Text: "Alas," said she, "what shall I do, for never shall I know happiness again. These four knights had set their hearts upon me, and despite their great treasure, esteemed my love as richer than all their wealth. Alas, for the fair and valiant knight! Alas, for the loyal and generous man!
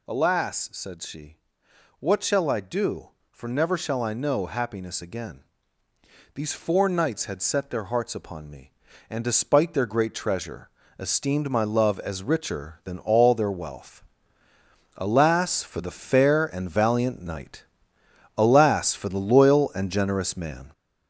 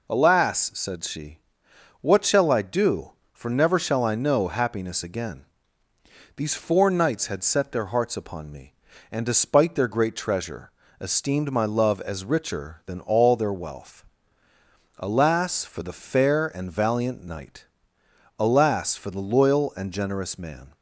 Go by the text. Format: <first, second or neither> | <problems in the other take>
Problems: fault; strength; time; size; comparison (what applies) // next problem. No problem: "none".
second | gets louder; noticeable; throughout; 5 dB